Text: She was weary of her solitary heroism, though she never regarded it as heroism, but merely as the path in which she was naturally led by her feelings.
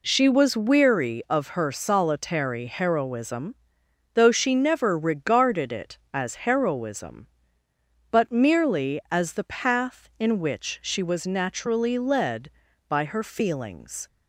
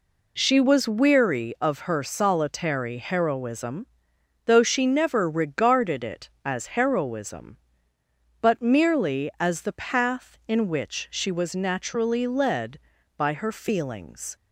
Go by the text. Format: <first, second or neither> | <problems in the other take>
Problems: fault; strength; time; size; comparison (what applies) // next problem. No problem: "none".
neither | none